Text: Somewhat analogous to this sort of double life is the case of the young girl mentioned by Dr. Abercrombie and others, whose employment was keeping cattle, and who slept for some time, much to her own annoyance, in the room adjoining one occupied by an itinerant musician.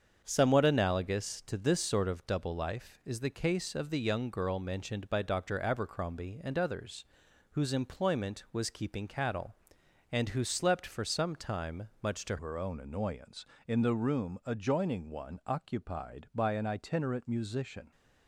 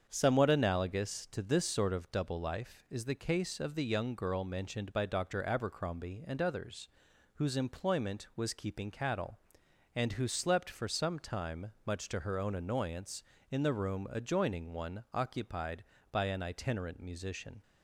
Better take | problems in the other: second | starts louder than the rest; strong; until 1.2 s; 7 dB; strong in the second // changes voice at "her"; from 12.3 s on; 5.6 s long

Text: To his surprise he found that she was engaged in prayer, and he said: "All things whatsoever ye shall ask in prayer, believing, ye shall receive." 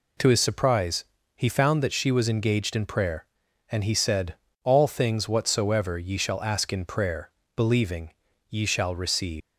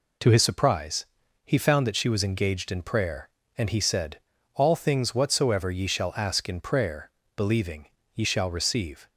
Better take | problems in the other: second | pauses between "surprise" and "he"; slight; at 1.0 s; 0.32 s long; also in the second // leaves "receive" unfinished; at 9.4 s; 180 ms

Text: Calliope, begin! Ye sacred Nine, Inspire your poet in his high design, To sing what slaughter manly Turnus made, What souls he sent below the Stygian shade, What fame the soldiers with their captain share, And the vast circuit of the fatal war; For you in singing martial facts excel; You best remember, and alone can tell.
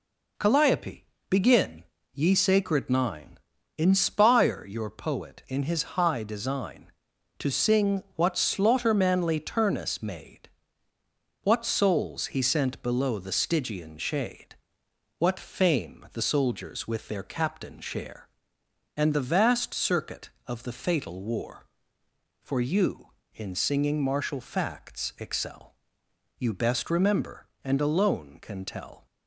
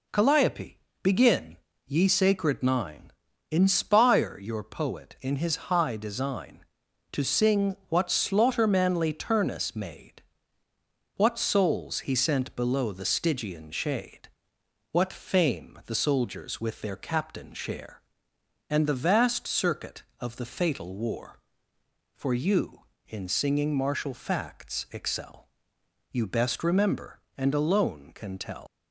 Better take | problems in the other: first | leaves "tell" unfinished; at 28.6 s; 115 ms

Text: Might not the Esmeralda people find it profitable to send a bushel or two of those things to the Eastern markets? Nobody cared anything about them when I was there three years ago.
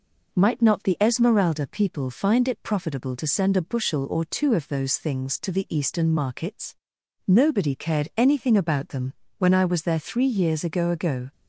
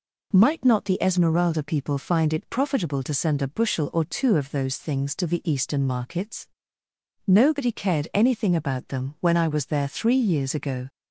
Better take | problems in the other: second | pauses between "them" and "when"; slight; at 9.1 s; 0.28 s long // says "ago" twice; at 10.8 s

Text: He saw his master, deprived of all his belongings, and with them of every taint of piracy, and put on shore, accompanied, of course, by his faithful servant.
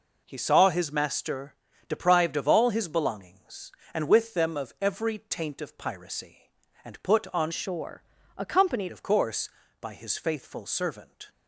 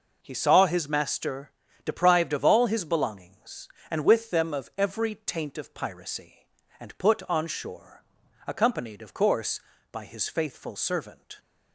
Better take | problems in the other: second | changes voice from "shore" to "accompanied"; from 7.5 to 8.9 s; 1.4 s long

